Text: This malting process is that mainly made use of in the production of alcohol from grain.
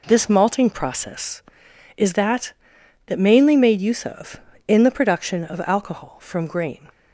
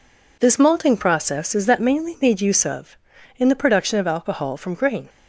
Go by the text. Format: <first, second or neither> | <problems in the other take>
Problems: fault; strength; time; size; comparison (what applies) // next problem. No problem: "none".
second | says "that" twice; at 3.0 s